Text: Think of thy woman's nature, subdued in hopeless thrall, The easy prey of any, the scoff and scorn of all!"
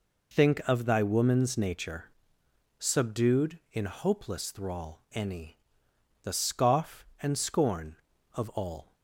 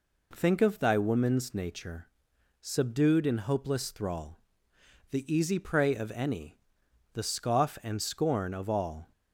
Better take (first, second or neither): second